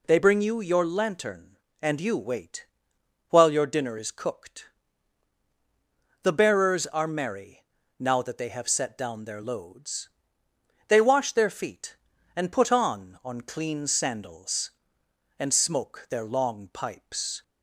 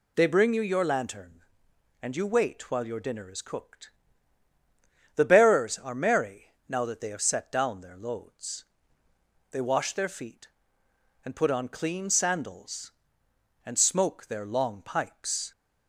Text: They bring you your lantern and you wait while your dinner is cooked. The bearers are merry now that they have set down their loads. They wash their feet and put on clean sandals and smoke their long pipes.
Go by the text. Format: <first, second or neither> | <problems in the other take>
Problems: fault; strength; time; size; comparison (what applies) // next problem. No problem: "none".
second | pauses between "wait" and "while"; noticeable; at 2.6 s; 0.64 s long // pauses between "merry" and "now"; slight; at 7.6 s; 0.34 s long; slight in the second // says "on" twice; at 13.2 s